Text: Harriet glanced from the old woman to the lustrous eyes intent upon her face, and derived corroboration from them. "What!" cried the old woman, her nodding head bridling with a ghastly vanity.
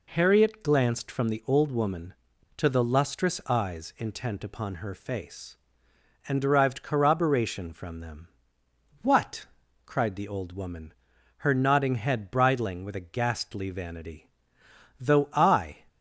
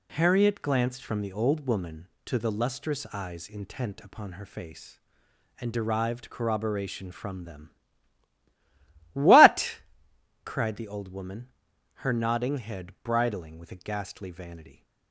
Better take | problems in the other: second | goes on to say "Though I"; noticeable; from 15.0 s on; 0.76 s long

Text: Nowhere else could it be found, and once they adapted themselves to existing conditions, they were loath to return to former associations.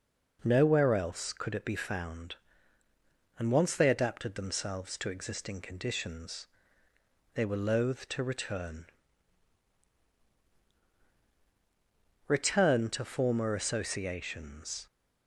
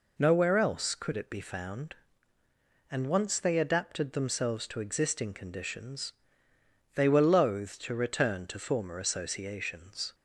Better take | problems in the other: second | says "return" twice; at 12.2 s

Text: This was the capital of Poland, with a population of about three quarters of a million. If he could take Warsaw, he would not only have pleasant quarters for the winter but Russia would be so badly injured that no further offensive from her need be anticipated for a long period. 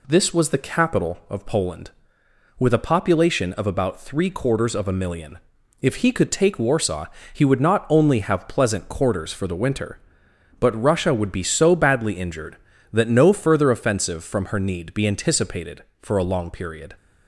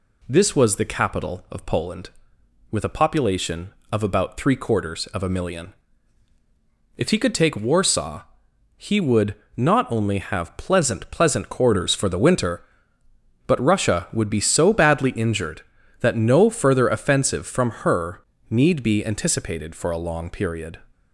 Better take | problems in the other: first | pauses between "would" and "not"; slight; at 9.3 s; 0.22 s long // says "pleasant" twice; at 11.1 s // pauses between "her" and "need"; slight; at 18.2 s; 0.26 s long

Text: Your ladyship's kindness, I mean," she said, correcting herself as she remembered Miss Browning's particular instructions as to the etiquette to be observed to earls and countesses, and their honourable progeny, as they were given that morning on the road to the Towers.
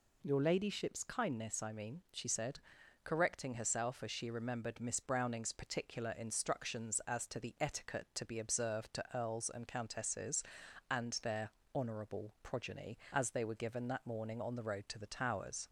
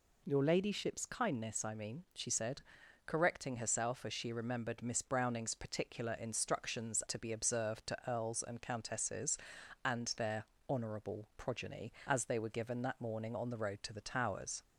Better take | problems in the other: first | skips "as to the etiquette"; at 7.0 s // pauses between "their" and "honourable"; slight; at 10.4 s; 0.24 s long; slight in the first

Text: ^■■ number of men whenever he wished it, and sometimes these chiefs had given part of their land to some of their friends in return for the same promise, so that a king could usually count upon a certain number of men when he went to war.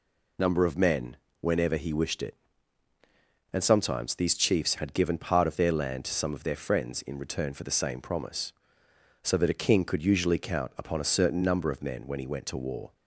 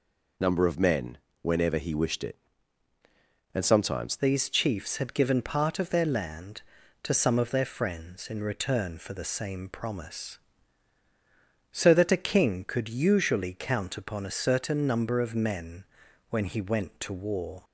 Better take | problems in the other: first | pauses between "men" and "whenever"; slight; at 1.1 s; 0.24 s long; slight in the first // changes voice at "these"; from 4.1 s on; 13.5 s long // pauses between "men" and "when"; noticeable; at 15.8 s; 0.46 s long

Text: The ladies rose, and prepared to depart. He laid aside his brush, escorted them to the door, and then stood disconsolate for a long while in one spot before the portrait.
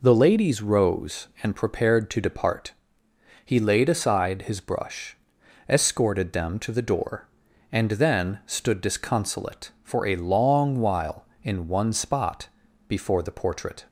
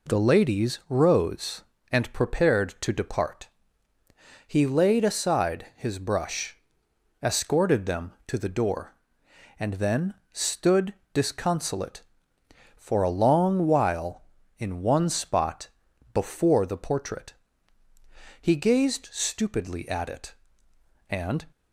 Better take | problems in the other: first | pauses between "then" and "stood"; slight; at 10.1 s; 0.18 s long // pauses between "stood" and "disconsolate"; slight; at 10.9 s; 0.20 s long // pauses between "spot" and "before"; at 15.6 s; 0.44 s long; also in the first // goes on to say "He gazed stupidly at it and"; strong; from 18.3 s on; 3.0 s long

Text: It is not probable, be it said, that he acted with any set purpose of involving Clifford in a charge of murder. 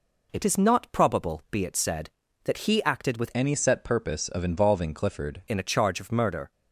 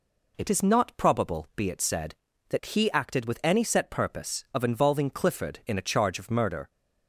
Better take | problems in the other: second | changes voice from "any" to "Clifford"; from 3.3 to 5.4 s; 2.1 s long

